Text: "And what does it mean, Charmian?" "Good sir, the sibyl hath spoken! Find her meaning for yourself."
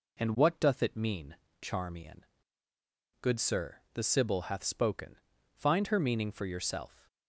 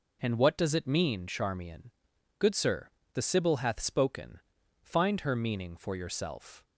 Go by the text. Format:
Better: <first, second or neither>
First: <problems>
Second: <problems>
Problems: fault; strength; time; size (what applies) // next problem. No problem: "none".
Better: second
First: says "doth" for "does"; at 0.5 s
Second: none